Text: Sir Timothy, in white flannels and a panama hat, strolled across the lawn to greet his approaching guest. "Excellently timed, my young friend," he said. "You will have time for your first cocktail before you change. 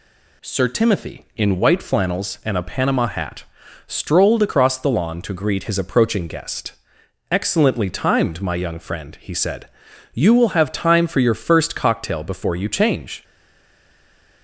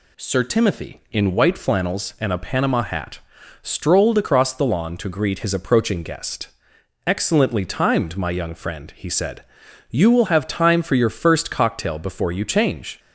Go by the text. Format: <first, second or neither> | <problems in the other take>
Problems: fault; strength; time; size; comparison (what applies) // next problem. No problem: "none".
second | stays silent after the last word; noticeable; from 13.2 s on; 1.2 s long